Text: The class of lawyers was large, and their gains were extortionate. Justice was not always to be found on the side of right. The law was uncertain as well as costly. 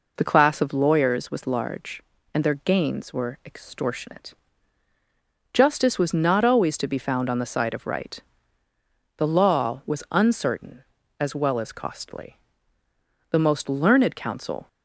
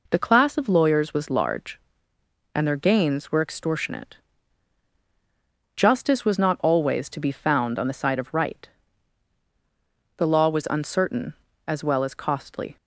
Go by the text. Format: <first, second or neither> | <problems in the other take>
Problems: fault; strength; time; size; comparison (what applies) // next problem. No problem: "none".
second | goes on to say "The most learned counsel"; from 13.3 s on; 1.3 s long